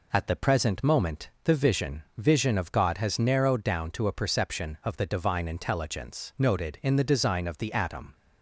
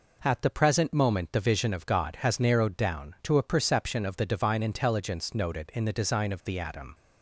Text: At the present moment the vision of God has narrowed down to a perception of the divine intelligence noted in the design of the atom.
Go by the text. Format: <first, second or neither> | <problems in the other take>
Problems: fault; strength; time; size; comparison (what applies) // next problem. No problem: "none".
second | says "vision" twice; at 2.1 s